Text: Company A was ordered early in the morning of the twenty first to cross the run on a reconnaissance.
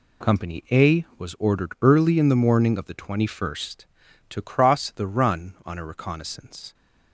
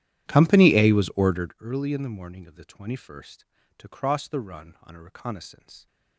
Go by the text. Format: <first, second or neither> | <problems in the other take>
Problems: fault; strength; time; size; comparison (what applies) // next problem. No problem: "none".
first | starts louder than the rest; strong; until 1.6 s; 11.5 dB